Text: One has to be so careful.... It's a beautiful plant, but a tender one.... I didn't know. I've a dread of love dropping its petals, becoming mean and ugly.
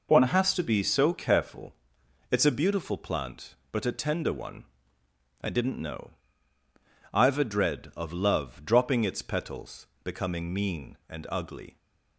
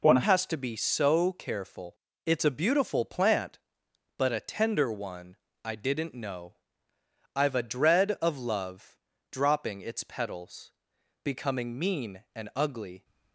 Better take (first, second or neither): first